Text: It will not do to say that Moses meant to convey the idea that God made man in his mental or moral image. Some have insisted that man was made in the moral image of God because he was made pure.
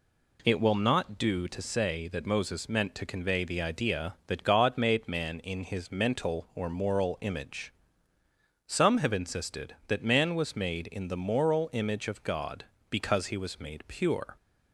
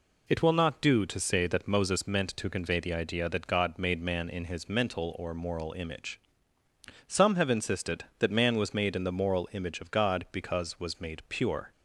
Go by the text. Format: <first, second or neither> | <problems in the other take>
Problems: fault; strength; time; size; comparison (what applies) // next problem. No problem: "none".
first | skips "he"; at 10.7 s